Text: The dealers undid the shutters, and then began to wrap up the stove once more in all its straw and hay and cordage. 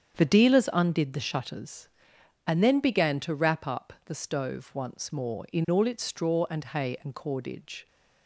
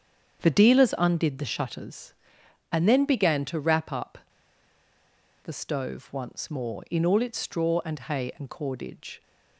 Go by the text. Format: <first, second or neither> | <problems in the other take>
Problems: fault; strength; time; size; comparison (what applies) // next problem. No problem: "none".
first | starts louder than the rest; strong; until 1.4 s; 7.5 dB; strong in the first // pauses between "up" and "the"; strong; at 4.1 s; 1.2 s long